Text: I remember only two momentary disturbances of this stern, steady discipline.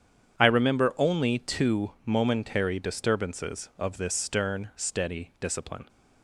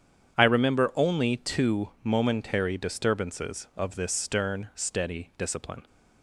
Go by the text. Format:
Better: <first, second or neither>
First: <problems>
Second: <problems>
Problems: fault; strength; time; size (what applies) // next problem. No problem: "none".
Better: neither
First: starts louder than the rest; strong; until 1.4 s; 8.5 dB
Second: starts louder than the rest; strong; until 1.4 s; 8.5 dB